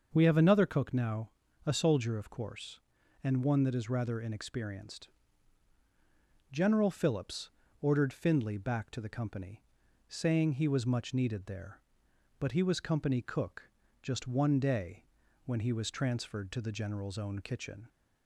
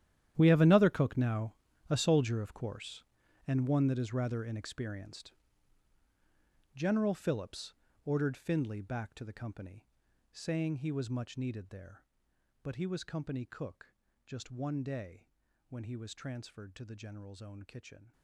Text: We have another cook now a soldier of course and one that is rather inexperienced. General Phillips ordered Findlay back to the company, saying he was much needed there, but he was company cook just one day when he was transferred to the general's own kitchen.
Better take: first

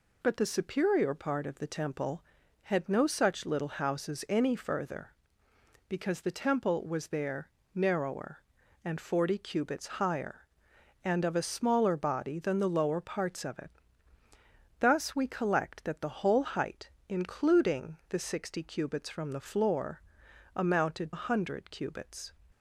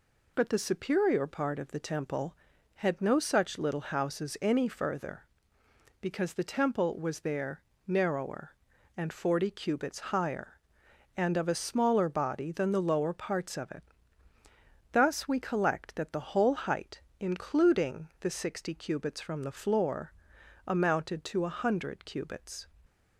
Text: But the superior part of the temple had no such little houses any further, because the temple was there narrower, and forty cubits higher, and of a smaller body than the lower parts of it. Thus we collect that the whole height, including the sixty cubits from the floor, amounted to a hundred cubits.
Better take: second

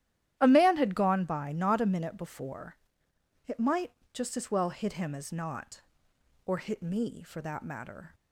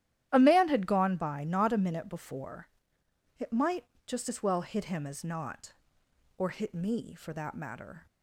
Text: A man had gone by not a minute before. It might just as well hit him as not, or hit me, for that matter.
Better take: neither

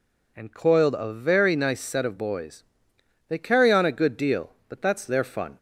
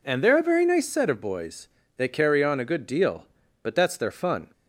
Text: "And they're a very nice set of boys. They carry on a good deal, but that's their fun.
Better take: second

